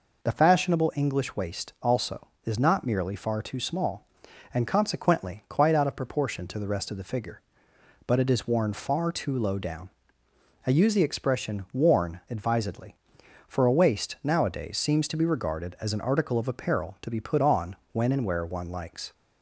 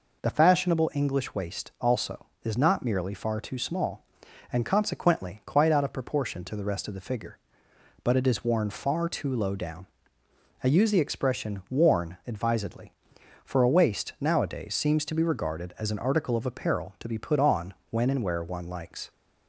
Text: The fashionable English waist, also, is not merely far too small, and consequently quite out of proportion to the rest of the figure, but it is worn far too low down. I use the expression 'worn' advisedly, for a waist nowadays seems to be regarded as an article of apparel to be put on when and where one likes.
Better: neither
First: pauses between "on" and "when"; slight; at 17.7 s; 0.16 s long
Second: pauses between "on" and "when"; slight; at 17.7 s; 0.16 s long

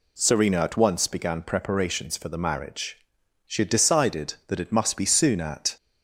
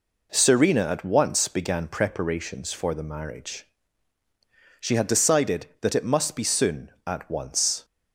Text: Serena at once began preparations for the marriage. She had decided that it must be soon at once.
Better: second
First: stops before "once"; at 5.7 s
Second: none

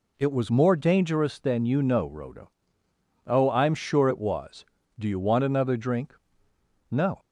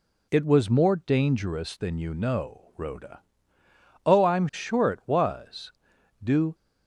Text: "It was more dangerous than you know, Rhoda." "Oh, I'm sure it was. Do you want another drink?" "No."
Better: first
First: none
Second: stops before "you want another drink No"; at 6.5 s

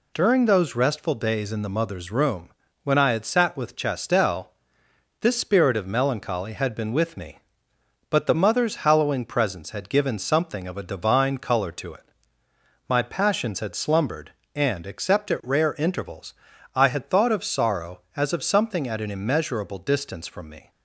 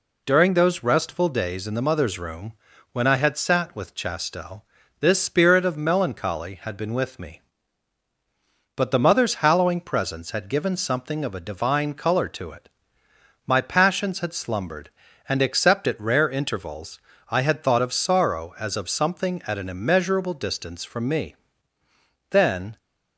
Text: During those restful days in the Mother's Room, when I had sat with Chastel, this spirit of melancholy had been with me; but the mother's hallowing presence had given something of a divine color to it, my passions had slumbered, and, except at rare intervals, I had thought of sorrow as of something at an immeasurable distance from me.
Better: first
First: none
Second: goes on to say "Then"; slight; from 22.2 s on; 0.48 s long

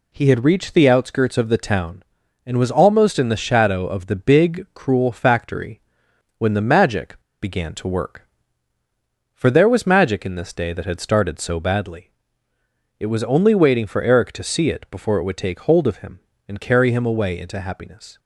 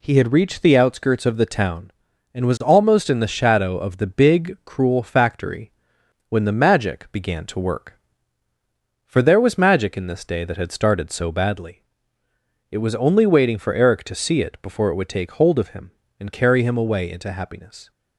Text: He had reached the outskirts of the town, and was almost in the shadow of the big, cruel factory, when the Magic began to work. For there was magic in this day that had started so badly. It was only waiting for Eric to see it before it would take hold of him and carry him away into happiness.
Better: second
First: pauses between "Magic" and "began"; slight; at 7.1 s; 0.22 s long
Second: none

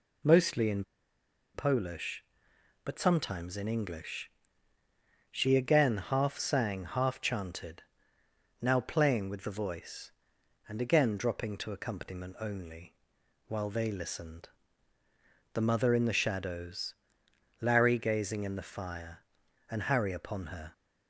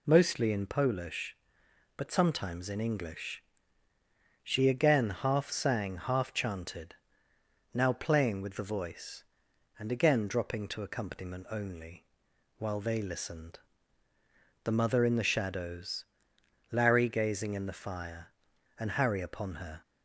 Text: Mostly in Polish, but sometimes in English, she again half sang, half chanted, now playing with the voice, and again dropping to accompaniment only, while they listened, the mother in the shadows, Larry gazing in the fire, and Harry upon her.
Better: second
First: pauses between "in" and "Polish"; noticeable; at 0.8 s; 0.72 s long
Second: none

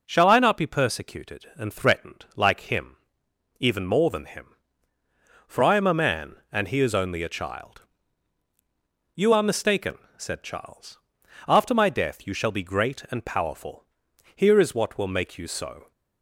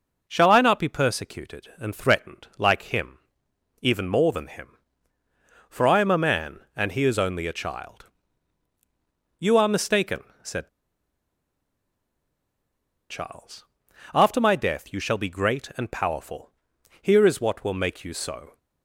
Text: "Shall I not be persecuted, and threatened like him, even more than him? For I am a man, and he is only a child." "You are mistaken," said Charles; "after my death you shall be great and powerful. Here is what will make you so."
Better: first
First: none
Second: pauses between "said" and "Charles"; strong; at 10.6 s; 2.4 s long

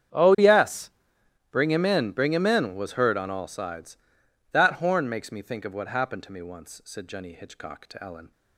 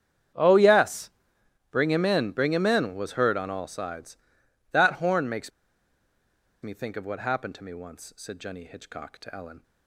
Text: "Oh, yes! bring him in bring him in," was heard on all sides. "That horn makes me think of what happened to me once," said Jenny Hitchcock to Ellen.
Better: first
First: starts louder than the rest; strong; until 1.8 s; 8.5 dB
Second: starts louder than the rest; strong; until 1.9 s; 9 dB // pauses between "makes" and "me"; at 5.5 s; 1.1 s long

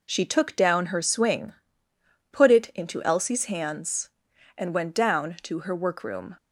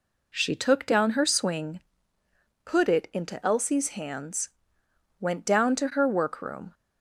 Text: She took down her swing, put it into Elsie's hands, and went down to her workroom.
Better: first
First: none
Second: skips "and"; at 4.8 s

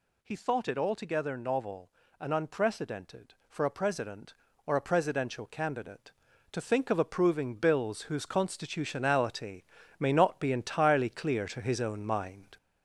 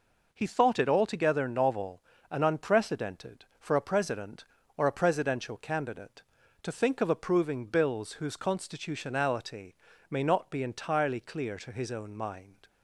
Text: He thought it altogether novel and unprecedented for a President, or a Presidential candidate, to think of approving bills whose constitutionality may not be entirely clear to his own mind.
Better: second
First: gets louder; noticeable; throughout; 4 dB // pauses between "constitutionality" and "may"; slight; at 9.6 s; 0.34 s long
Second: pauses between "constitutionality" and "may"; slight; at 9.7 s; 0.34 s long

